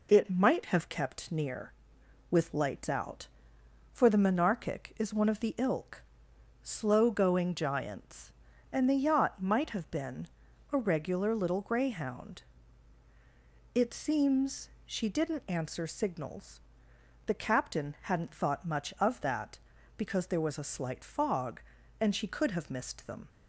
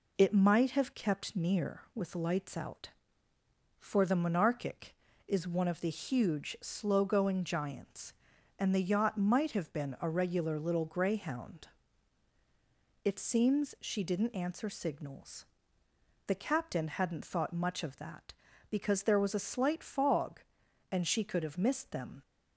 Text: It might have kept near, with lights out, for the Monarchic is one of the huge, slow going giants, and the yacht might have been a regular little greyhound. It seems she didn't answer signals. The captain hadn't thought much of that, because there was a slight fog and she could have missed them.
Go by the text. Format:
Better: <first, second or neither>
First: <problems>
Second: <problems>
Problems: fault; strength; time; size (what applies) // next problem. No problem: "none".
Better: second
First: says "ilk" for "huge"; at 5.5 s // pauses between "been" and "a"; noticeable; at 10.2 s; 0.46 s long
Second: none